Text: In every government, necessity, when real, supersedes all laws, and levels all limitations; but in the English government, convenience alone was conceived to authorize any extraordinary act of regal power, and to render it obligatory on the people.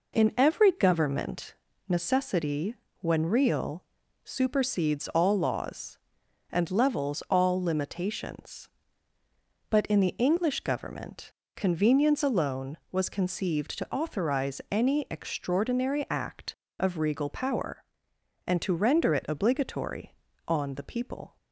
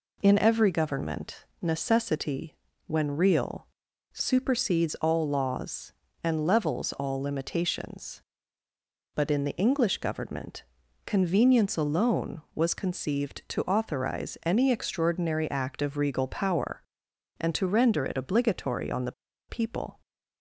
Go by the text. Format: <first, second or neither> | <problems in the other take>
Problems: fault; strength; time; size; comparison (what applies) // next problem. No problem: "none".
first | pauses between "the" and "people"; at 19.1 s; 0.36 s long